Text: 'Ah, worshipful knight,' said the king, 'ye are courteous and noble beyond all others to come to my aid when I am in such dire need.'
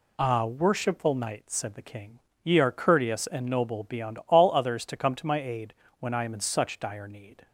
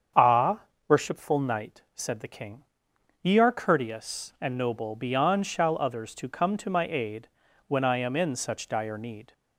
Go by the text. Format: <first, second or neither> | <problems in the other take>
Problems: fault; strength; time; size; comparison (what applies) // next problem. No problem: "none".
first | starts louder than the rest; strong; until 1.4 s; 7.5 dB // says "shall" for "all"; at 5.4 s // pauses between "aid" and "when"; at 7.2 s; 0.40 s long; slight in the first